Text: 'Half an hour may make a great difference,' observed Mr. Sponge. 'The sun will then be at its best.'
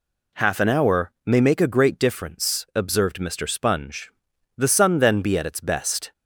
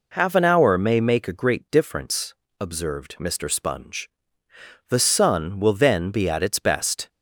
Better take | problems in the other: second | skips "will"; at 4.9 s

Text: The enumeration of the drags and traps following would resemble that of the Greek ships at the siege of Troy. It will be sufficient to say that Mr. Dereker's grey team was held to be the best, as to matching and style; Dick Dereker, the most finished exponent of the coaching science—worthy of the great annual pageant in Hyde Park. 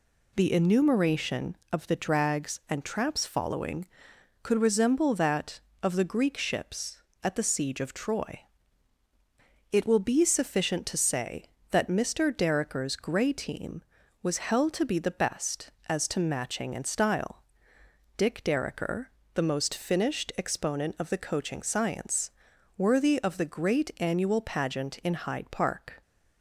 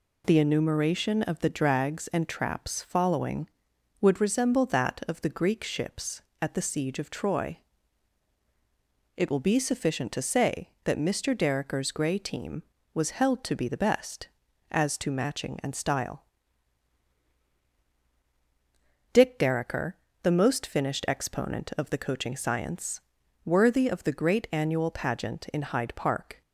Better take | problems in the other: second | says "could" for "would"; at 4.4 s

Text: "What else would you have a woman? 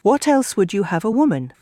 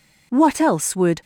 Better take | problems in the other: first | stops before "you have a woman"; at 1.2 s

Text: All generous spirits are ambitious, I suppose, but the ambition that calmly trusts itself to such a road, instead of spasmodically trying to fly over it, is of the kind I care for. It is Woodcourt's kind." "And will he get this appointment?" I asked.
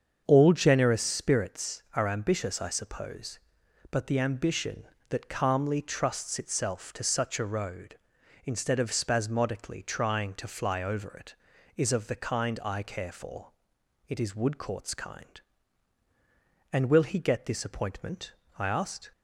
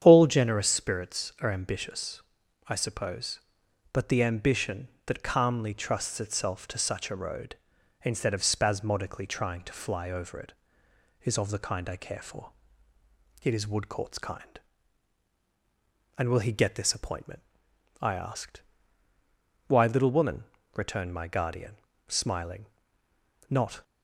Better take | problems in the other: first | starts louder than the rest; strong; until 1.0 s; 9 dB; also in the first // goes on to say "Why little woman returned my guardian smiling not"; strong; from 19.6 s on; 4.1 s long

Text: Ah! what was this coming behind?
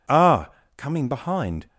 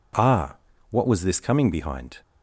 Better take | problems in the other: second | skips "what was this"; at 0.6 s

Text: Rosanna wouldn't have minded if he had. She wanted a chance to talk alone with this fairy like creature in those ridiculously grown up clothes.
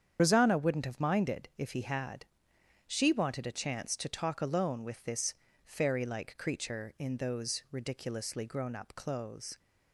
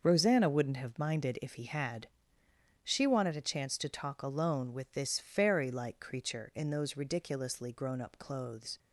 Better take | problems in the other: second | loses the start of "Rosanna"; at 0.1 s; 55 ms // starts louder than the rest; strong; until 1.2 s; 8 dB; also in the second // pauses between "this" and "fairy"; slight; at 5.3 s; 0.30 s long

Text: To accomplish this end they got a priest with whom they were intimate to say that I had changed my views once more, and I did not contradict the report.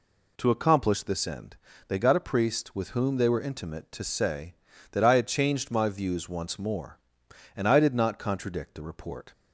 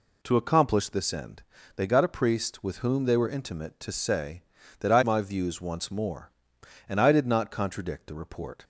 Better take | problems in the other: first | pauses between "end" and "they"; slight; at 1.4 s; 0.34 s long; slight in the first // skips "had changed"; at 5.0 s

